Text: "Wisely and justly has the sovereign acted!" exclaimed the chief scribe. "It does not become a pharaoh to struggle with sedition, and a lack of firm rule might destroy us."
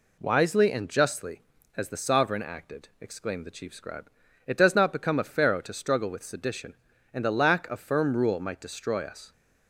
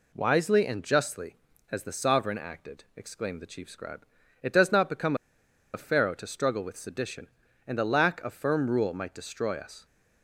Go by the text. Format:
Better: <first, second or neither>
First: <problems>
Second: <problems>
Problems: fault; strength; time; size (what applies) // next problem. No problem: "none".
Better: first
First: none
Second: pauses between "become" and "a"; noticeable; at 5.1 s; 0.59 s long